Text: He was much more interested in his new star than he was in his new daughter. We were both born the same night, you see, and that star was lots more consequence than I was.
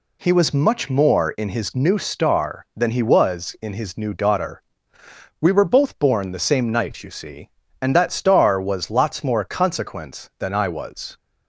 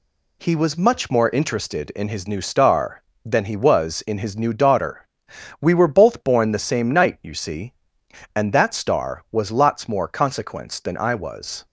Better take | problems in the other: second | skips "interested"; at 1.3 s

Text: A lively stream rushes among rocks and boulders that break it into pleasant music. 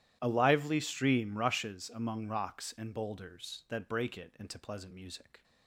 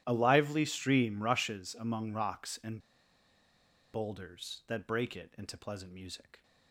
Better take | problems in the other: first | starts louder than the rest; strong; until 1.0 s; 12 dB; strong in the first // pauses between "and" and "boulders"; at 2.7 s; 1.1 s long

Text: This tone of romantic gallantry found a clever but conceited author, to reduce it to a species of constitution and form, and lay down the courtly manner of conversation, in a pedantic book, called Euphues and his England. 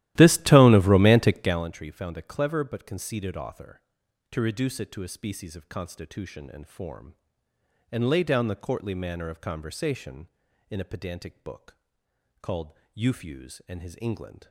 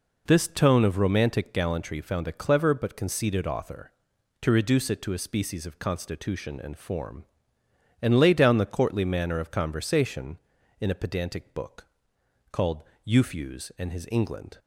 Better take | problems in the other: second | starts louder than the rest; strong; until 1.7 s; 15 dB // pauses between "called" and "Euphues"; slight; at 12.7 s; 0.22 s long; slight in the second

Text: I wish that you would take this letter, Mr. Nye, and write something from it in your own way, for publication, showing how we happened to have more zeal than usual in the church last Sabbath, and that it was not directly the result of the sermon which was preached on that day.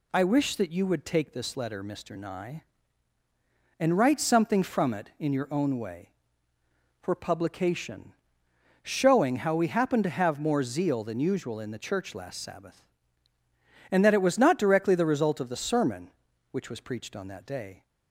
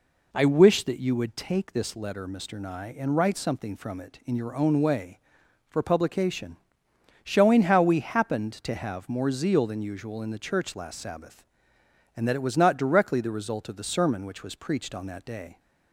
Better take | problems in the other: neither | none

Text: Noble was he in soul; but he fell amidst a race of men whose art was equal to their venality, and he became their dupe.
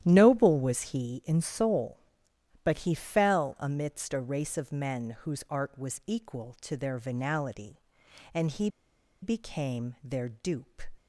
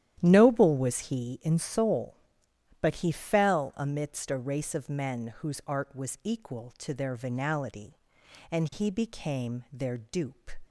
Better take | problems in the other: second | starts louder than the rest; strong; until 1.0 s; 11.5 dB; strong in the second // pauses between "he" and "became"; noticeable; at 8.6 s; 0.54 s long

